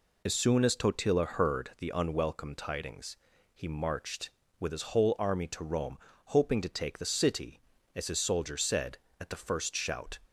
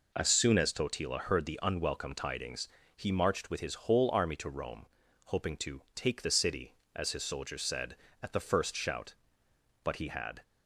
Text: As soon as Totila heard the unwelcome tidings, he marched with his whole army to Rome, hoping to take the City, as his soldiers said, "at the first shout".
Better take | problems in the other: first | goes on to say "But he had"; from 9.8 s on; 0.60 s long

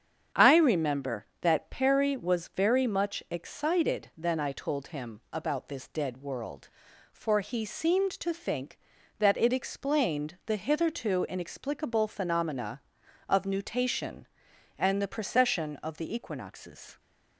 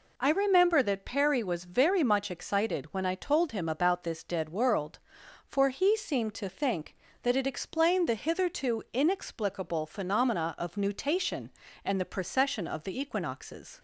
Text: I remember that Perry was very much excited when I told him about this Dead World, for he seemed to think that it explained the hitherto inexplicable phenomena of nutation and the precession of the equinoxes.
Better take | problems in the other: second | starts louder than the rest; strong; until 1.5 s; 8 dB // says "then" for "when"; at 4.1 s

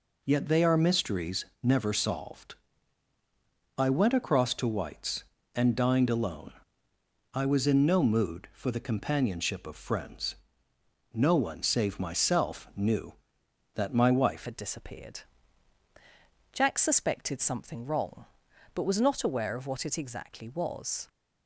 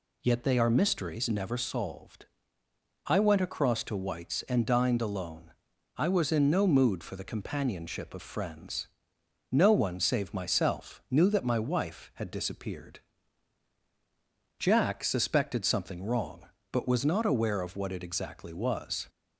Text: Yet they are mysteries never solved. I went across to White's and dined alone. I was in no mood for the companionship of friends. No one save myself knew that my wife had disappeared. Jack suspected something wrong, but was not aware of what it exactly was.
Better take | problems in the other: second | pauses between "mysteries" and "never"; slight; at 1.4 s; 0.18 s long // changes voice at "had"; from 14.4 s on; 6.6 s long

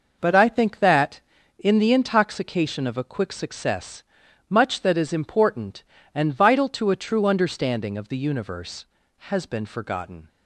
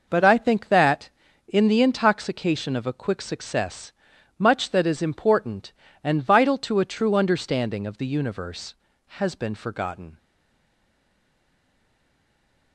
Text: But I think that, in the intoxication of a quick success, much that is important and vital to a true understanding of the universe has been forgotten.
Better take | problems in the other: first | stays silent after the last word; strong; from 10.1 s on; 2.6 s long

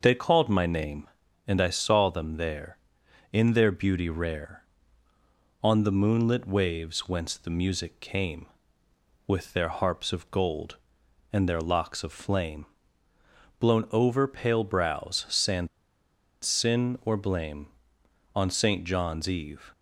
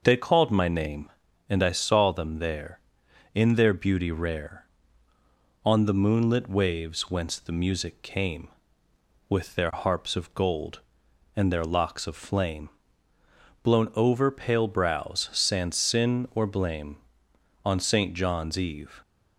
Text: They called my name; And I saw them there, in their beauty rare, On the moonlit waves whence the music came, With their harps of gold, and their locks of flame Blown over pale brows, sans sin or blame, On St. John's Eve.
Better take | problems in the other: second | pauses between "flame" and "Blown"; noticeable; at 12.6 s; 0.94 s long; noticeable in the second // pauses between "sans" and "sin"; noticeable; at 15.6 s; 0.76 s long

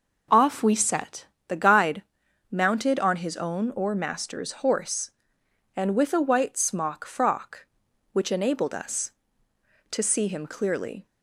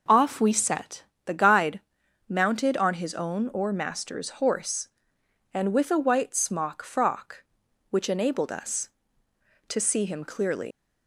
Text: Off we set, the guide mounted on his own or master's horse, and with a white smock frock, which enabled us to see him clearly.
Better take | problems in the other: first | pauses between "guide" and "mounted"; noticeable; at 1.8 s; 0.48 s long; noticeable in the first // leaves "clearly" unfinished; at 10.7 s; 120 ms

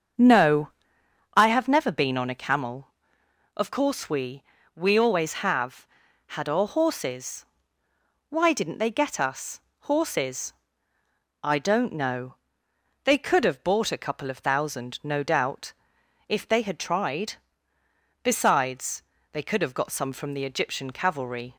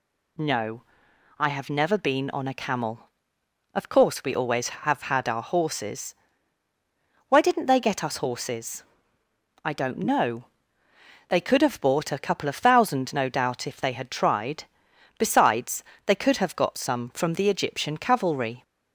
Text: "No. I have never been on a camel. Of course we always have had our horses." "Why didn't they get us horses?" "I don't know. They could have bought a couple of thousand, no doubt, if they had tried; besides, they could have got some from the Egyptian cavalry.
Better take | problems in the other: second | starts louder than the rest; until 1.8 s; 7 dB // says "we" twice; at 4.7 s // pauses between "us" and "horses"; slight; at 9.5 s; 0.20 s long

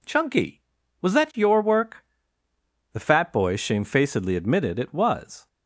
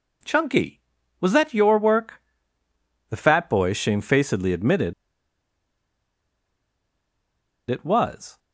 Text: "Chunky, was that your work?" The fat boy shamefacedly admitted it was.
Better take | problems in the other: first | pauses between "admitted" and "it"; strong; at 4.9 s; 2.7 s long

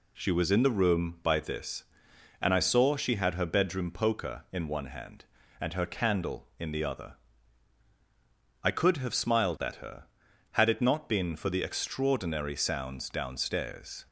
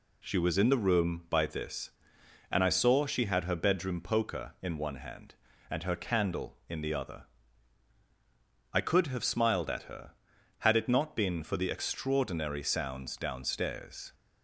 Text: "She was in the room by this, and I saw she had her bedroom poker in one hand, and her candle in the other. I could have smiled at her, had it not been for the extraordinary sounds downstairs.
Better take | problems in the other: neither | none

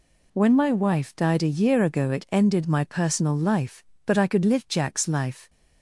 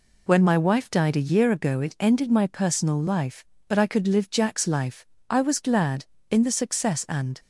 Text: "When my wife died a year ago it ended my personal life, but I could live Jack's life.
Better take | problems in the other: first | goes on to say "I was glad in the success and"; strong; from 5.2 s on; 2.1 s long

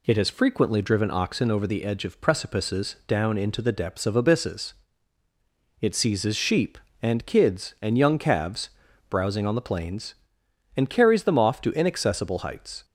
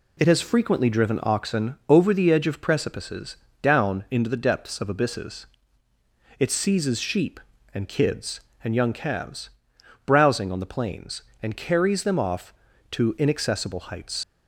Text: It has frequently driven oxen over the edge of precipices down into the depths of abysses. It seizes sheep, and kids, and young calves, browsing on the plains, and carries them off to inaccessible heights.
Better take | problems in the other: first | pauses between "precipices" and "down"; slight; at 3.3 s; 0.26 s long // leaves "heights" unfinished; at 14.2 s; 80 ms

